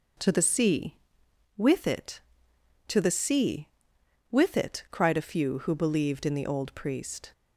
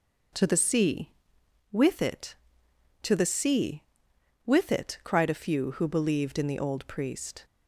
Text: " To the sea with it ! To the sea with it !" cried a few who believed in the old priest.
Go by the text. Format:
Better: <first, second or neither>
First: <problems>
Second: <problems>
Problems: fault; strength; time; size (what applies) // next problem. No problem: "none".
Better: neither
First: starts louder than the rest; noticeable; until 1.7 s; 6 dB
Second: starts louder than the rest; noticeable; until 1.9 s; 6 dB